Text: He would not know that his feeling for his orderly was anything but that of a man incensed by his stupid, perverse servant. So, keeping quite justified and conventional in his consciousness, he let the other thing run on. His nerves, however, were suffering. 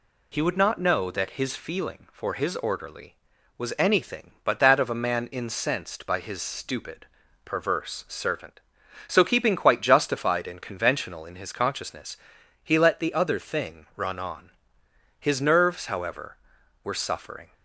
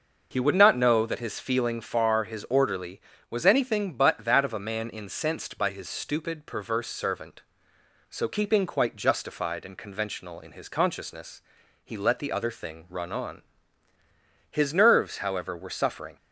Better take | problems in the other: first | starts louder than the rest; noticeable; until 1.3 s; 6 dB // says "far" for "for"; at 1.8 s

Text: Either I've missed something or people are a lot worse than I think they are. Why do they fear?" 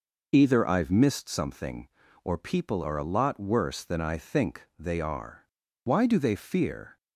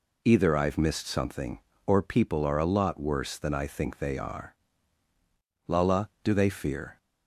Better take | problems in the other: first | says "Lala" for "Why"; at 5.6 s

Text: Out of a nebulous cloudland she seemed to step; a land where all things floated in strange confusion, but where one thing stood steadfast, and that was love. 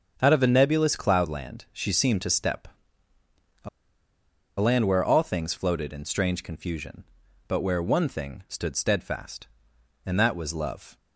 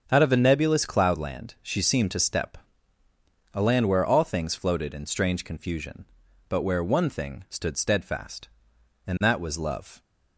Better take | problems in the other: second | starts louder than the rest; strong; until 1.2 s; 7.5 dB; strong in the second // pauses between "a" and "land"; noticeable; at 3.6 s; 0.91 s long

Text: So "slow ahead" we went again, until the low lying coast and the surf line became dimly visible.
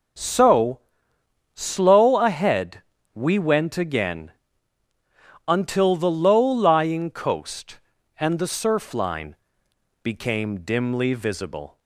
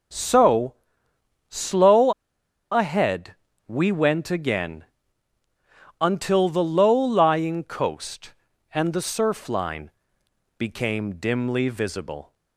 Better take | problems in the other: first | pauses between "So" and "slow"; noticeable; at 0.7 s; 0.74 s long; noticeable in the first // pauses between "slow" and "ahead"; noticeable; at 2.1 s; 0.59 s long // pauses between "ahead" and "we"; slight; at 3.3 s; 0.32 s long; slight in the first // pauses between "line" and "became"; noticeable; at 9.9 s; 0.68 s long; noticeable in the first

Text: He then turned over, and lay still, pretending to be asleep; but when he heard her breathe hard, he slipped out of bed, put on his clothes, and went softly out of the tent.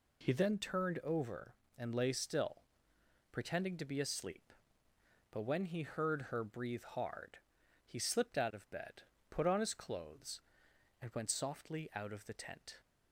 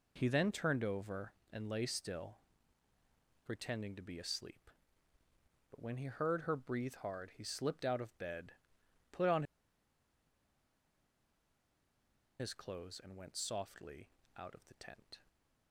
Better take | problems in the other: first | pauses between "on" and "his"; strong; at 9.4 s; 2.9 s long // pauses between "softly" and "out"; slight; at 14.0 s; 0.30 s long

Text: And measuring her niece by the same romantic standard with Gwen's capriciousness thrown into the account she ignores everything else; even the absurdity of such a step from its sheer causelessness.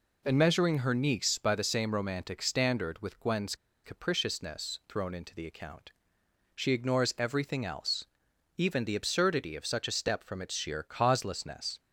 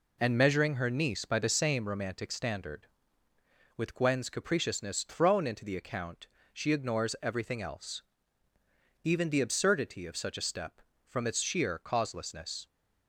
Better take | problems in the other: second | pauses between "Gwen's" and "capriciousness"; slight; at 3.5 s; 0.30 s long // pauses between "account" and "she"; noticeable; at 5.9 s; 0.62 s long; slight in the second

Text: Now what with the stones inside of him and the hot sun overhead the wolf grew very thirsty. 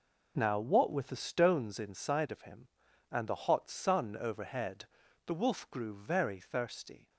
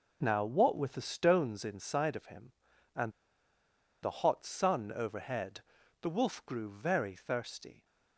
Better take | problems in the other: first | pauses between "and" and "the"; noticeable; at 3.1 s; 0.91 s long // pauses between "overhead" and "the"; at 5.6 s; 0.40 s long; also in the first

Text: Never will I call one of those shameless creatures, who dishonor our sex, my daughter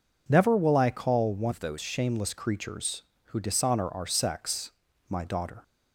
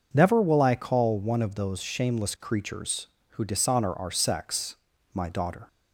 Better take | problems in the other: second | changes voice from "of" to "those"; from 1.5 to 1.7 s; 0.2 s long

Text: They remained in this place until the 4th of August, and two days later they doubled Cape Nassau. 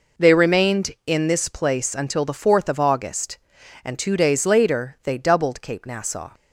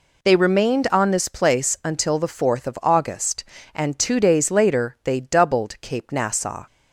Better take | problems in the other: first | says "on" for "in"; at 0.9 s

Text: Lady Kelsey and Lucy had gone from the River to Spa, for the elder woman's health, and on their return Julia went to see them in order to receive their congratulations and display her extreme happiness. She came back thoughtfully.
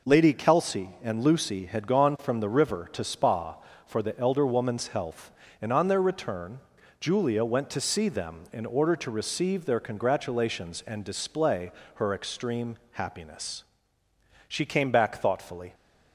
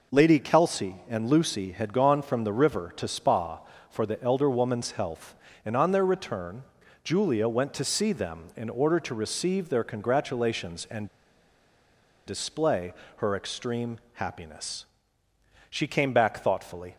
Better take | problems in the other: first | pauses between "return" and "Julia"; at 6.6 s; 0.42 s long; also in the first // pauses between "and" and "display"; at 11.0 s; 1.1 s long // pauses between "display" and "her"; slight; at 12.9 s; 0.24 s long; slight in the first

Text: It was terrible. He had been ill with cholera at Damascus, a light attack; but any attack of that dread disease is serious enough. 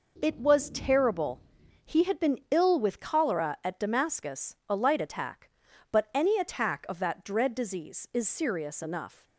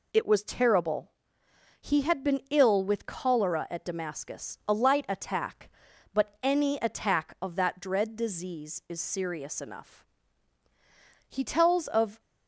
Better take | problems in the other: first | goes on to say "He tells of"; noticeable; from 11.2 s on; 0.92 s long

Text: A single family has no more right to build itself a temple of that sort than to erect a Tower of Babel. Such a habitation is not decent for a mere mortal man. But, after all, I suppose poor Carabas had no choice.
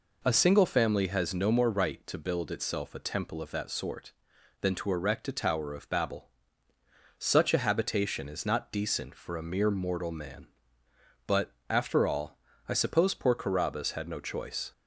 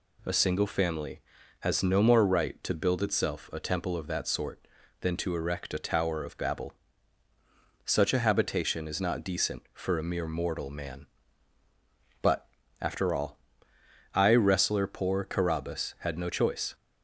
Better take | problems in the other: first | says "wrestler" for "suppose"; at 14.3 s

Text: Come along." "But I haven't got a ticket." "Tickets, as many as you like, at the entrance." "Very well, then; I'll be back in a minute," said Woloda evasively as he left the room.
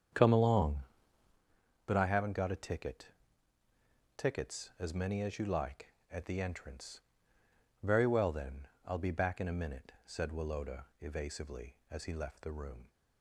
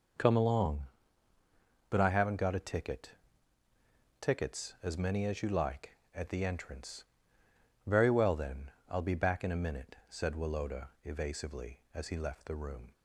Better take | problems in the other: second | starts louder than the rest; strong; until 1.4 s; 8 dB // pauses between "Woloda" and "evasively"; slight; at 10.8 s; 0.16 s long; slight in the second

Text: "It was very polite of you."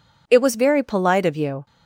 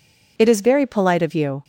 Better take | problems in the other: first | says "is" for "was"; at 0.4 s

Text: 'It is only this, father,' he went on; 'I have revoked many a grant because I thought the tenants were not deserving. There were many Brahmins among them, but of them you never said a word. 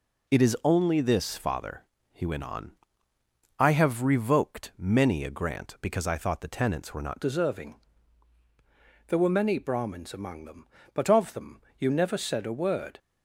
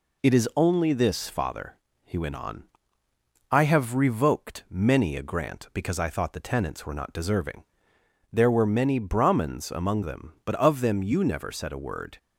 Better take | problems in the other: second | changes voice at "deserving"; from 7.2 s on; 5.7 s long // pauses between "them" and "you"; slight; at 11.6 s; 0.18 s long

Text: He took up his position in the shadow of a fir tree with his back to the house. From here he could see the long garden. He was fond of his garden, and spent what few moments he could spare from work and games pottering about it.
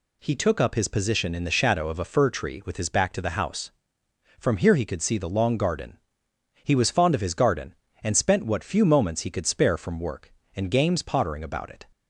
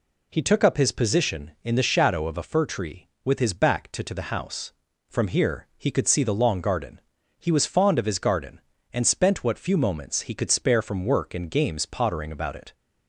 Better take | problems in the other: first | says "to" twice; at 4.0 s

